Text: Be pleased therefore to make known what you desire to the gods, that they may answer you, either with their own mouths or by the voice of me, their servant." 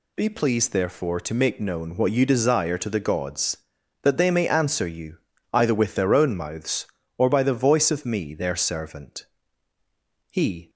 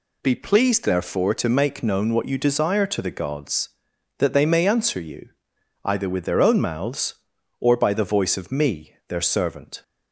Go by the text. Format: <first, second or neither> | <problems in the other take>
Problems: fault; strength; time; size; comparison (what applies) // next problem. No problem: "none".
second | goes on to say "He"; slight; from 10.2 s on; 0.40 s long